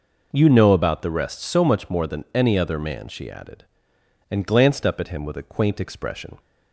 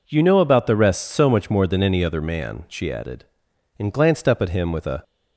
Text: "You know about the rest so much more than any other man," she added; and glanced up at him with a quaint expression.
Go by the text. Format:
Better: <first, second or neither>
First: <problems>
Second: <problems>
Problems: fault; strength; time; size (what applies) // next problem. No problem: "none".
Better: first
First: none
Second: stops before "quaint expression"; at 5.0 s